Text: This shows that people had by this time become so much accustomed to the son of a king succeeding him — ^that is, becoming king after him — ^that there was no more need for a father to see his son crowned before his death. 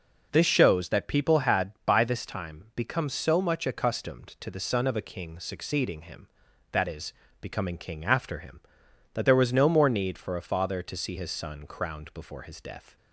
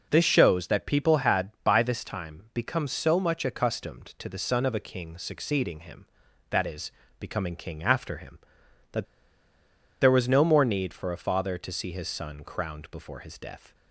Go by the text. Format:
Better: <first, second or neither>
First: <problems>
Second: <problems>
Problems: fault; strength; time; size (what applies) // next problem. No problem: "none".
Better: first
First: none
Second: pauses between "that" and "there"; noticeable; at 9.0 s; 0.96 s long